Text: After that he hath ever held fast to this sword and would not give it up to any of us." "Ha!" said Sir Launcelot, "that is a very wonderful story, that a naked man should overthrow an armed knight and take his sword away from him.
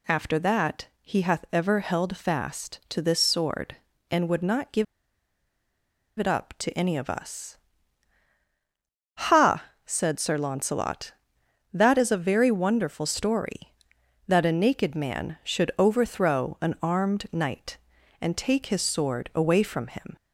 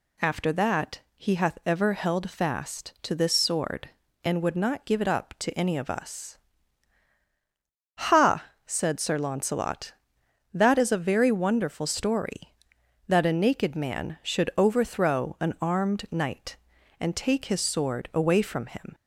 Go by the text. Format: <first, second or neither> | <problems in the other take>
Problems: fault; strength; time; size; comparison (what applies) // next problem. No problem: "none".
second | pauses between "give" and "it"; strong; at 4.8 s; 1.3 s long